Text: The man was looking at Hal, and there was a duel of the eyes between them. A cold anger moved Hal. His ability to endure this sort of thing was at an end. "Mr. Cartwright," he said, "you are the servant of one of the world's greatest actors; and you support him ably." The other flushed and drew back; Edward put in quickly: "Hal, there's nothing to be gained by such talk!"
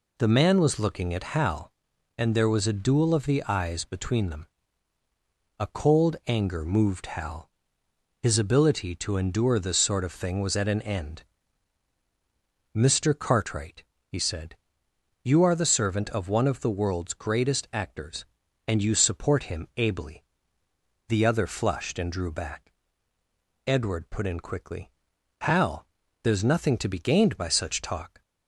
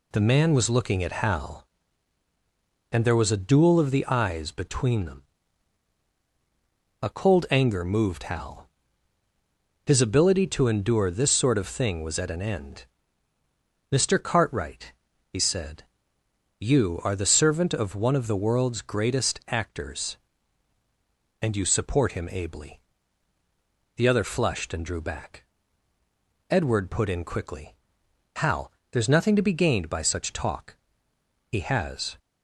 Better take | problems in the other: first | goes on to say "He has"; noticeable; from 31.4 s on; 0.70 s long

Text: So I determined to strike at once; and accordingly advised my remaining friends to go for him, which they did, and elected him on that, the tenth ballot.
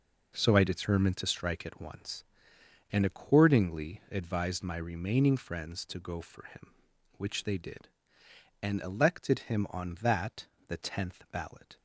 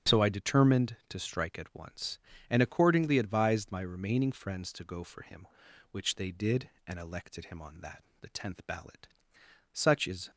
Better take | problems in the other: first | starts louder than the rest; strong; until 1.2 s; 8 dB // goes on to say "Such is"; from 9.7 s on; 0.56 s long

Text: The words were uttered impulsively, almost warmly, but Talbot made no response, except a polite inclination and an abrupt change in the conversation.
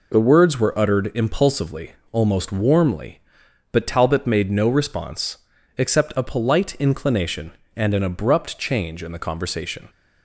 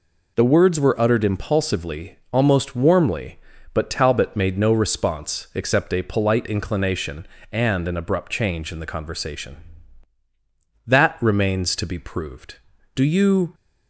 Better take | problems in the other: first | goes on to say "That remains to be proved Do you"; strong; from 10.8 s on; 2.6 s long

